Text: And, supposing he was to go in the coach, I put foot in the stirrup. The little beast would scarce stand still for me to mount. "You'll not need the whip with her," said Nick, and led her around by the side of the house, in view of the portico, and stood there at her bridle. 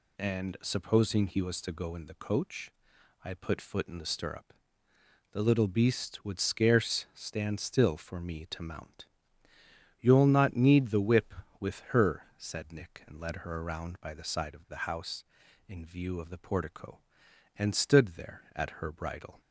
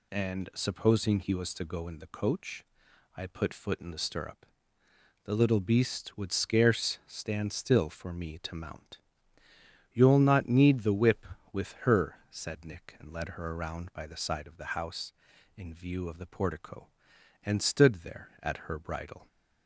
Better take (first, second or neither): neither